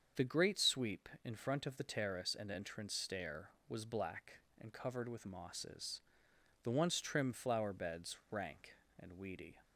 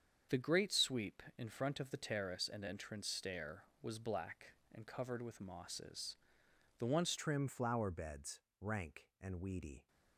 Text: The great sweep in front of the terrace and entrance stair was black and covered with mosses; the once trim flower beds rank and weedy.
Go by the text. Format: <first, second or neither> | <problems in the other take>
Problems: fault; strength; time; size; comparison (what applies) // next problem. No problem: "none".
first | starts louder than the rest; strong; until 1.4 s; 7 dB; also in the first // changes voice at "trim"; from 7.1 s on; 2.7 s long // pauses between "beds" and "rank"; slight; at 8.4 s; 0.18 s long